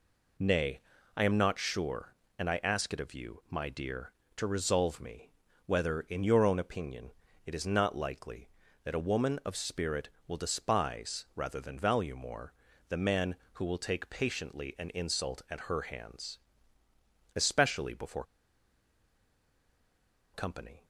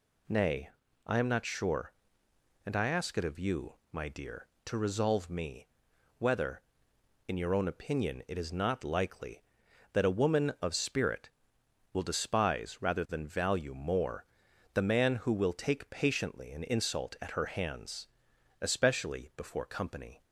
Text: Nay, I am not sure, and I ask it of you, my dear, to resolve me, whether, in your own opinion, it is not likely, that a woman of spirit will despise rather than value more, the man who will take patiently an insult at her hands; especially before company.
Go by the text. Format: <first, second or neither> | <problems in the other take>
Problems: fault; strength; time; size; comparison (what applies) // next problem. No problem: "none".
second | pauses between "before" and "company"; strong; at 18.2 s; 2.1 s long